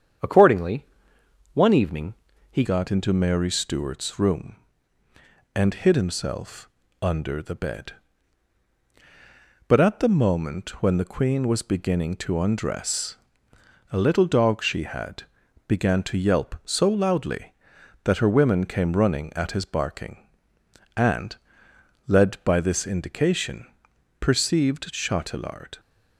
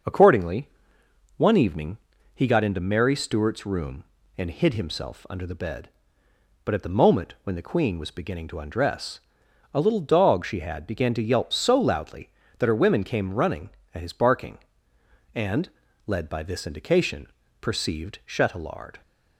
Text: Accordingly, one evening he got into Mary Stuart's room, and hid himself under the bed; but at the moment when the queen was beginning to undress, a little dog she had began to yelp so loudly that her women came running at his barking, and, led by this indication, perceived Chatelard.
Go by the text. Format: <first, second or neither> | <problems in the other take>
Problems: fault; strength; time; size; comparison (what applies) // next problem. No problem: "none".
second | starts louder than the rest; strong; until 1.9 s; 8 dB; noticeable in the second // pauses between "evening" and "he"; at 2.1 s; 0.38 s long; also in the second // changes voice at "got"; from 2.6 s on; 23.1 s long // pauses between "himself" and "under"; slight; at 6.6 s; 0.32 s long // pauses between "had" and "began"; at 15.2 s; 0.42 s long